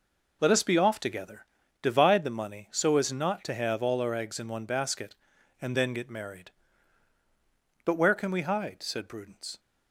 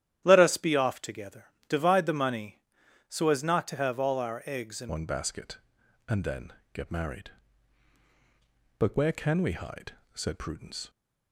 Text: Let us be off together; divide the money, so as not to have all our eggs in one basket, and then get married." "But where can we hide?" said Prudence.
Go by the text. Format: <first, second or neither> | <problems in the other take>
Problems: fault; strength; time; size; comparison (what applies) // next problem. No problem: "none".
first | starts louder than the rest; strong; until 1.2 s; 11.5 dB // changes voice at "one"; from 4.8 s on; 6.0 s long // pauses between "then" and "get"; slight; at 6.5 s; 0.20 s long